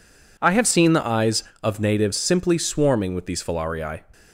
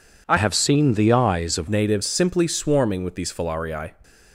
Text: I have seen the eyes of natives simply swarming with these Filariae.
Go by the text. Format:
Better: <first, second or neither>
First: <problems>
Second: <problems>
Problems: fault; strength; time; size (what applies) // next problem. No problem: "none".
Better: first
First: none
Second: changes voice from "have" to "of"; from 0.3 to 1.6 s; 1.3 s long